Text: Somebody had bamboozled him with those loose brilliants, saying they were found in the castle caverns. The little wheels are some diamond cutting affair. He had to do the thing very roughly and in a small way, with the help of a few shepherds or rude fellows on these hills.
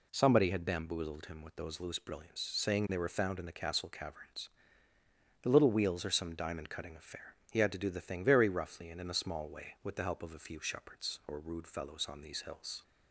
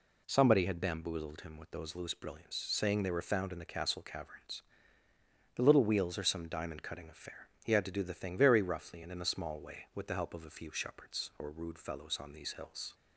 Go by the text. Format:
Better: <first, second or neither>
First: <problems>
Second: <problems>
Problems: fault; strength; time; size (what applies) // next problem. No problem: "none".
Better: neither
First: none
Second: none